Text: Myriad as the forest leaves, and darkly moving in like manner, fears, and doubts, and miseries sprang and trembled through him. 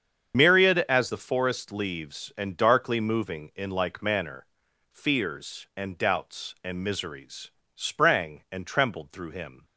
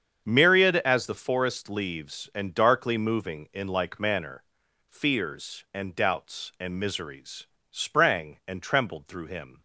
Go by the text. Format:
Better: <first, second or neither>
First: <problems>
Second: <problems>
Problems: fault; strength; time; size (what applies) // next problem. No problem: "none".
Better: second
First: loses the start of "Myriad"; at 0.3 s; 70 ms // starts louder than the rest; strong; until 1.4 s; 7.5 dB // pauses between "miseries" and "sprang"; slight; at 7.5 s; 0.24 s long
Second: starts louder than the rest; strong; until 1.2 s; 7.5 dB // pauses between "miseries" and "sprang"; slight; at 7.4 s; 0.24 s long